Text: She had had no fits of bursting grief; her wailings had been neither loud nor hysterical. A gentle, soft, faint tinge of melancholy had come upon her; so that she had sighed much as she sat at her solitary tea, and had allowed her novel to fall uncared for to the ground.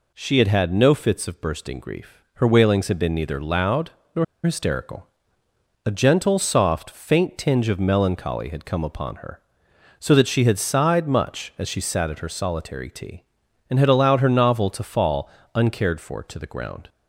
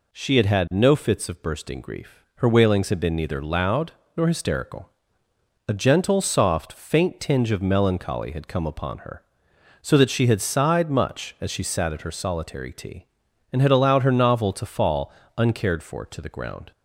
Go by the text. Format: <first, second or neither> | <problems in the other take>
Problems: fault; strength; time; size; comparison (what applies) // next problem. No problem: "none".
second | pauses between "loud" and "nor"; slight; at 3.8 s; 0.24 s long; slight in the second // pauses between "nor" and "hysterical"; slight; at 4.2 s; 0.21 s long // pauses between "fall" and "uncared"; slight; at 15.2 s; 0.26 s long; slight in the second